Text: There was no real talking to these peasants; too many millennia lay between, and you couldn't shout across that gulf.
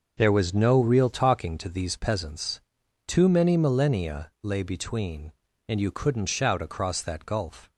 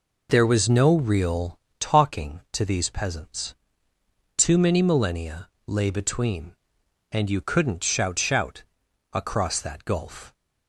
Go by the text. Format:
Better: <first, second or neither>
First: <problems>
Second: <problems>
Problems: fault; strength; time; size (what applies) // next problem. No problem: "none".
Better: first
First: none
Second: pauses between "real" and "talking"; slight; at 1.5 s; 0.22 s long // pauses between "millennia" and "lay"; slight; at 5.4 s; 0.18 s long // says "shout" twice; at 8.1 s